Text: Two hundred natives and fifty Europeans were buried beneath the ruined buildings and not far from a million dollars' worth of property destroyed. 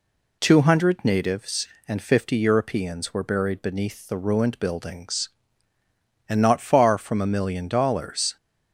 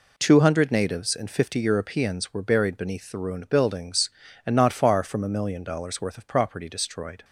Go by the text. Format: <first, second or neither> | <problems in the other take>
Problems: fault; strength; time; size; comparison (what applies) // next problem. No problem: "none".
second | stops before "worth of property destroyed"; at 8.3 s